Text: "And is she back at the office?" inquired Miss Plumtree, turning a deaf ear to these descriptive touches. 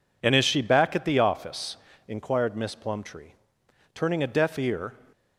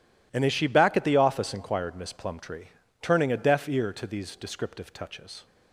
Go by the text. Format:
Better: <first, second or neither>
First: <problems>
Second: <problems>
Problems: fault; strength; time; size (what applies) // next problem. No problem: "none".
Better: second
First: stops before "to these descriptive touches"; at 5.1 s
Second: none